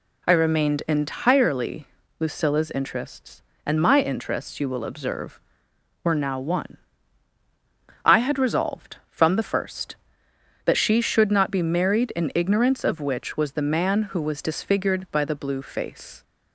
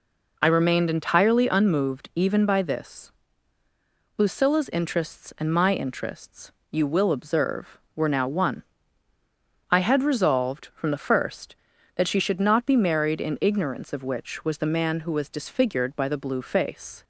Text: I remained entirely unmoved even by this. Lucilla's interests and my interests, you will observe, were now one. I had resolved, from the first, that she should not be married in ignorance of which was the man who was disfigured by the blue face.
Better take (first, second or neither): second